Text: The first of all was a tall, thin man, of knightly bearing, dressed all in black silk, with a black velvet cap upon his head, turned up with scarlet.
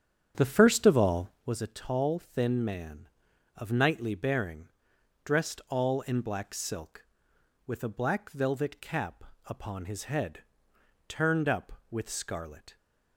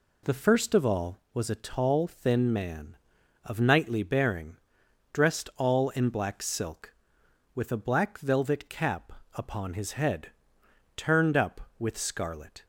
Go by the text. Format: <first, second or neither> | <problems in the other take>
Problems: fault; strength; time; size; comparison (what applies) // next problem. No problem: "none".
second | starts louder than the rest; strong; until 1.5 s; 8.5 dB // pauses between "cap" and "upon"; slight; at 9.2 s; 0.22 s long; slight in the second